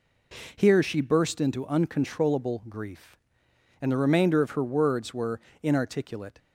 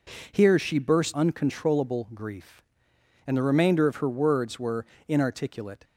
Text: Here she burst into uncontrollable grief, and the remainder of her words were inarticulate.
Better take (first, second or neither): first